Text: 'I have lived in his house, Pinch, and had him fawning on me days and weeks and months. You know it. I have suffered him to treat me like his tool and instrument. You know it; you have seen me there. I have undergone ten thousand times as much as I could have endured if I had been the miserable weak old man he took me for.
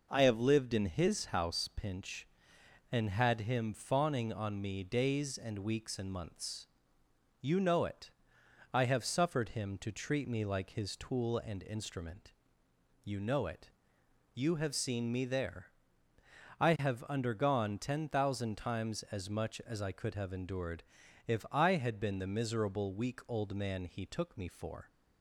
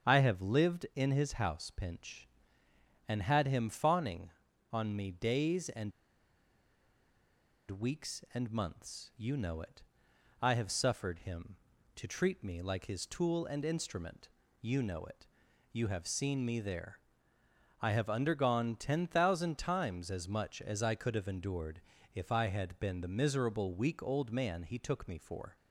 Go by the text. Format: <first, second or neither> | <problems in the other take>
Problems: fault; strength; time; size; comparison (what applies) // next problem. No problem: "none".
first | starts louder than the rest; strong; until 1.1 s; 7.5 dB // pauses between "and" and "weeks"; strong; at 5.9 s; 1.8 s long // pauses between "endured" and "if"; slight; at 21.7 s; 0.32 s long; also in the first